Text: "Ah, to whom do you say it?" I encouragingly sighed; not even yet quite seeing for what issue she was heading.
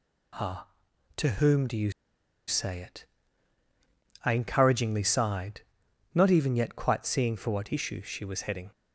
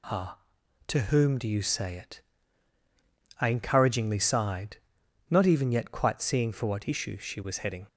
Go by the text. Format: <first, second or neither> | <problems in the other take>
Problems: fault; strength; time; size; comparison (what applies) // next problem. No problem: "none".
second | pauses between "you" and "say"; noticeable; at 1.9 s; 0.55 s long